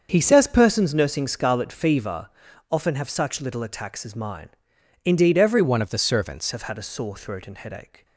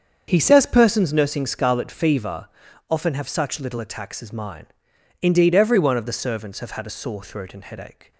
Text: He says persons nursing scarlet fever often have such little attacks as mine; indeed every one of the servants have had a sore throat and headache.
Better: second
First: starts louder than the rest; until 1.1 s; 7 dB // pauses between "fever" and "often"; at 2.3 s; 0.38 s long // changes voice from "one" to "servants"; from 5.6 to 6.5 s; 0.9 s long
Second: starts louder than the rest; strong; until 1.2 s; 7 dB // pauses between "fever" and "often"; at 2.4 s; 0.38 s long

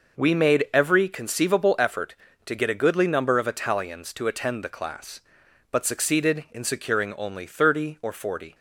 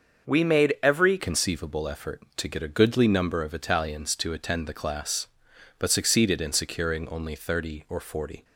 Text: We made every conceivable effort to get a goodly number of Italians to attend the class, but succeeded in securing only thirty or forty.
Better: first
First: none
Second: starts louder than the rest; until 1.3 s; 6 dB // changes voice at "conceivable"; from 1.1 s on; 7.3 s long

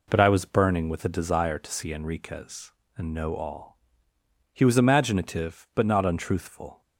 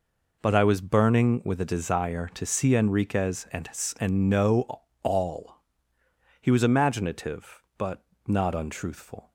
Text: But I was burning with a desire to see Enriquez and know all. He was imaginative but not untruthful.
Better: first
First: none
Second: says "and" twice; at 3.9 s // pauses between "know" and "all"; slight; at 4.8 s; 0.20 s long // pauses between "but" and "not"; slight; at 8.0 s; 0.22 s long

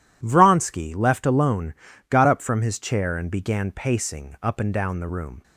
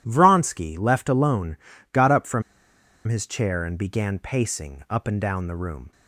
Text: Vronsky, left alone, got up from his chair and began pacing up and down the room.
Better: first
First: none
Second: pauses between "from" and "his"; noticeable; at 2.4 s; 0.64 s long

